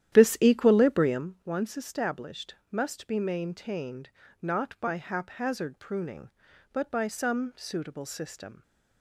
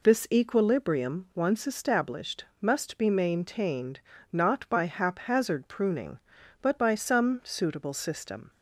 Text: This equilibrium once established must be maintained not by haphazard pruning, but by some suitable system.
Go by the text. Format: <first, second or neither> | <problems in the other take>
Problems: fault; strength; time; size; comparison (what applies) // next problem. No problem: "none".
second | starts louder than the rest; strong; until 1.3 s; 11.5 dB // pauses between "established" and "must"; slight; at 2.5 s; 0.16 s long; slight in the second // pauses between "maintained" and "not"; slight; at 4.1 s; 0.32 s long; slight in the second